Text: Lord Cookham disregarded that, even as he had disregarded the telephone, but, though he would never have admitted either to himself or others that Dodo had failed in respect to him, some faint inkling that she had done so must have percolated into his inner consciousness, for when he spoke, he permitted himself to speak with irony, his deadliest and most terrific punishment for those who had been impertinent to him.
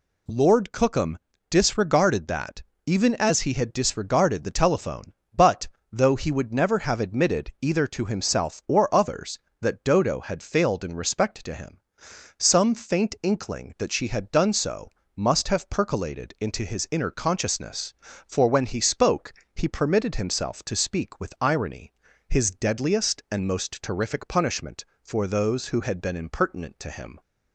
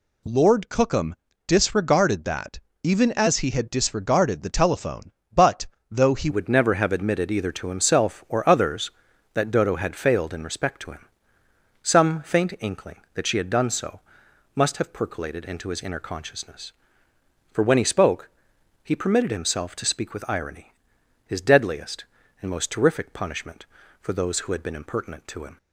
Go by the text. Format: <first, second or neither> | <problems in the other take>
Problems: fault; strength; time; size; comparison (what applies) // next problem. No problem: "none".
first | pauses between "Cookham" and "disregarded"; slight; at 1.1 s; 0.32 s long; slight in the first // changes voice at "would"; from 6.2 s on; 19.3 s long // pauses between "so" and "must"; noticeable; at 13.9 s; 0.56 s long; slight in the first